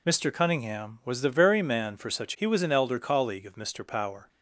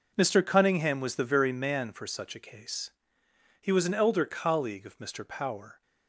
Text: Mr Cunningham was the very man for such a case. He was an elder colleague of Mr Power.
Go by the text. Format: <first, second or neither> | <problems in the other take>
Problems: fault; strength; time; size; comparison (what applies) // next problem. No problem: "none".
second | skips "a case"; at 2.3 s